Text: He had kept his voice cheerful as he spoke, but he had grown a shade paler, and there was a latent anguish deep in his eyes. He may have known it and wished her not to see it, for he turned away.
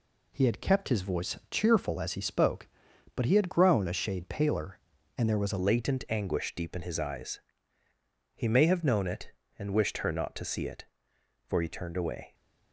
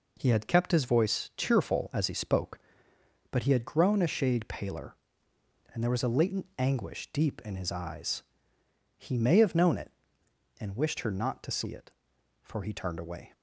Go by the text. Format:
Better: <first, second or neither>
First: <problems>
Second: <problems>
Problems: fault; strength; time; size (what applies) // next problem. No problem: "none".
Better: second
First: changes voice at "latent"; from 5.5 s on; 6.8 s long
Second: none